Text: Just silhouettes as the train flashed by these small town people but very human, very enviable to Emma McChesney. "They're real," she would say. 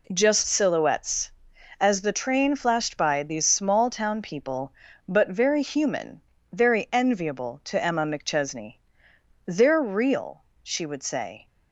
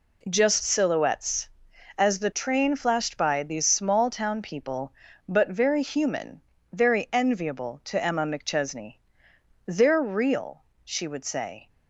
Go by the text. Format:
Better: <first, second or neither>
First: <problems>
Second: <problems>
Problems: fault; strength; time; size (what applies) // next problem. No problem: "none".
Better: neither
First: none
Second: none